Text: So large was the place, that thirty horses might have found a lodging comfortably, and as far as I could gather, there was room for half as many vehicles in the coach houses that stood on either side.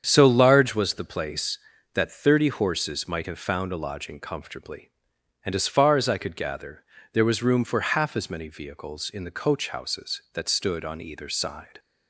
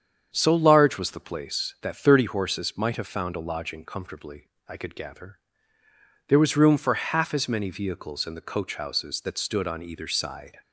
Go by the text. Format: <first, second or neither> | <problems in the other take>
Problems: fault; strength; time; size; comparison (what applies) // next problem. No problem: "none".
first | starts louder than the rest; strong; until 1.3 s; 7.5 dB; strong in the first // skips "and as far as"; at 4.5 s